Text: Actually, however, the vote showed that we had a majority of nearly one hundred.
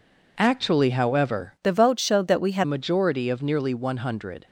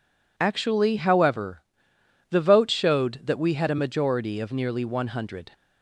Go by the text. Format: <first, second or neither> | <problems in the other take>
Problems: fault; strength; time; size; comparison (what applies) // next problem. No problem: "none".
second | changes voice from "the" to "had"; from 1.6 to 2.6 s; 1.0 s long